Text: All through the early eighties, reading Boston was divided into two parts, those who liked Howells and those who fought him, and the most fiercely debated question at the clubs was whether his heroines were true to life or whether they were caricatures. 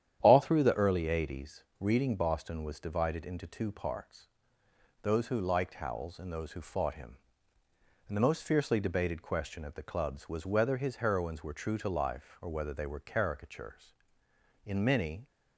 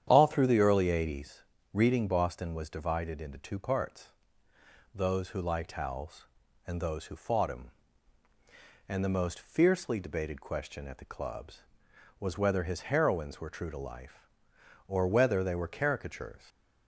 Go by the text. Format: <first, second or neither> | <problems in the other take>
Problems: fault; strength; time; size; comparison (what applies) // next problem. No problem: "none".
second | starts louder than the rest; strong; until 1.2 s; 10 dB; strong in the second // goes on to say "In many"; noticeable; from 14.6 s on; 0.62 s long